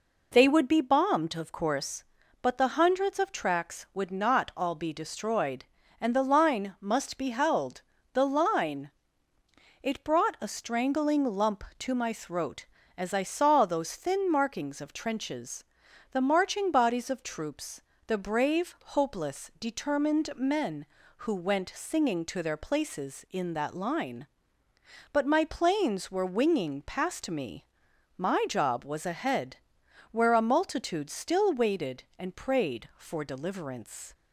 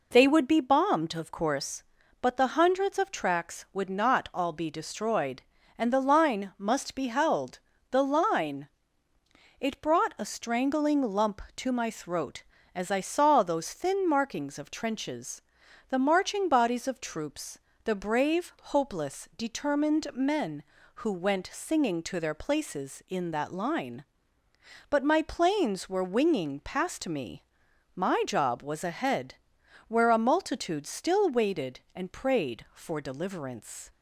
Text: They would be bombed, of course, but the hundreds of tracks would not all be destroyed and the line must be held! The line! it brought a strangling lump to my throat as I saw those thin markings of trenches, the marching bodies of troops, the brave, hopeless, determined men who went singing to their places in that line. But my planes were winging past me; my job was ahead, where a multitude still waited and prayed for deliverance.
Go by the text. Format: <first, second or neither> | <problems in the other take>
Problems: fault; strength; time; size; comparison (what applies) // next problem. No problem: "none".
neither | none